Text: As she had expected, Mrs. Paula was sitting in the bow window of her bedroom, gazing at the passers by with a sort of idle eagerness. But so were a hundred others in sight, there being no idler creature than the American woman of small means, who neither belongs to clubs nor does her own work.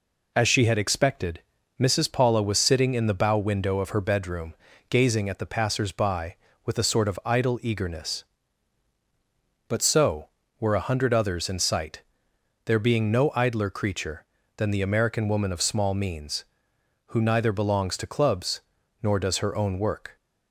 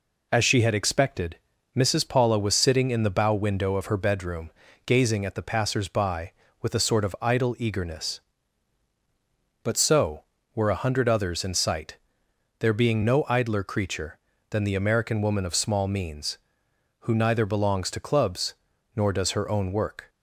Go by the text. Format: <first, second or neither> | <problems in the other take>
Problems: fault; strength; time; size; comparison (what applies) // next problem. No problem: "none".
neither | pauses between "clubs" and "nor"; the same in both